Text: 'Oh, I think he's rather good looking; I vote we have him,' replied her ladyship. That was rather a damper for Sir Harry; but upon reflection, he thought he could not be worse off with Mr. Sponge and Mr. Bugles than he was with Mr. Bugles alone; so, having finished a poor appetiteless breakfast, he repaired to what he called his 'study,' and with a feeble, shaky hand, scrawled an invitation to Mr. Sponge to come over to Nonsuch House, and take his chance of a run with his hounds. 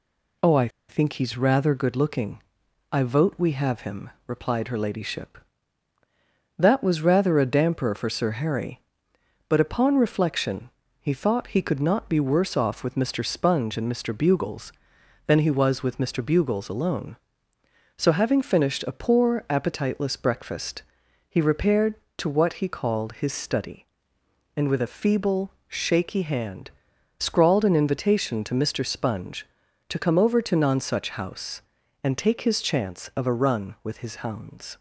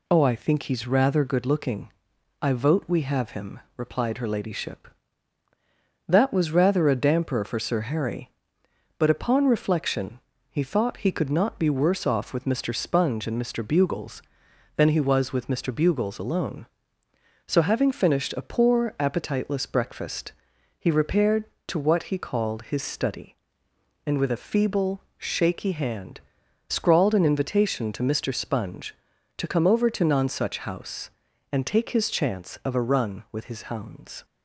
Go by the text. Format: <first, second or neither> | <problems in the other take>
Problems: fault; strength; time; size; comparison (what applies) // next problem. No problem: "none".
second | pauses between "I" and "think"; slight; at 0.6 s; 0.20 s long